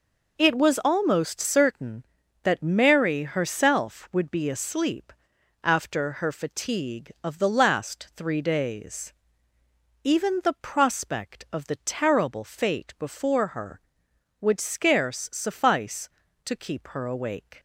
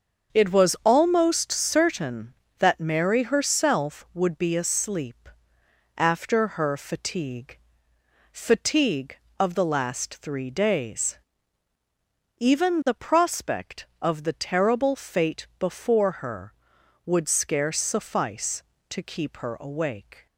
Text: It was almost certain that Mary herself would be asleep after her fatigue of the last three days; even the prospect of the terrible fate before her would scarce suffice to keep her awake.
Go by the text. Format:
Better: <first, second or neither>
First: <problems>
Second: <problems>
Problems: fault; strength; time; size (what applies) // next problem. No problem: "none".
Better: first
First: pauses between "asleep" and "after"; noticeable; at 5.1 s; 0.50 s long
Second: starts louder than the rest; until 1.4 s; 6.5 dB // pauses between "asleep" and "after"; noticeable; at 5.2 s; 0.70 s long // says "fatigue" twice; at 8.3 s